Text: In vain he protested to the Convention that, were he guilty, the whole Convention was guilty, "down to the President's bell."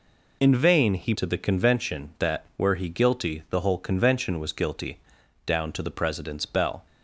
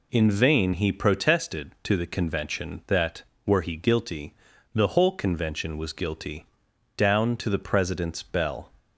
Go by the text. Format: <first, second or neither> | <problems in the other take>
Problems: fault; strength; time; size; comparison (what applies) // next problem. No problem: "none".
second | skips "protested"; at 1.1 s